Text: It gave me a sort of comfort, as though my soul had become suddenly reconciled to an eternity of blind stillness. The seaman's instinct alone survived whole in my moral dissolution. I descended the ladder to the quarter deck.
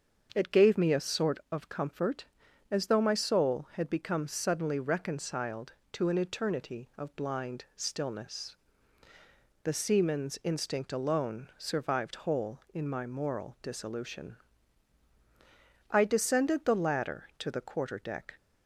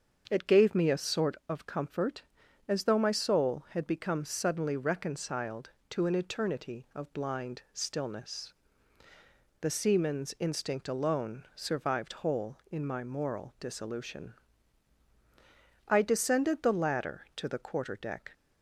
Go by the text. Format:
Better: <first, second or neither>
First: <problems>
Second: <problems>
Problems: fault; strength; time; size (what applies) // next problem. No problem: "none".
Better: neither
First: starts louder than the rest; until 1.3 s; 7 dB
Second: starts louder than the rest; until 1.3 s; 7 dB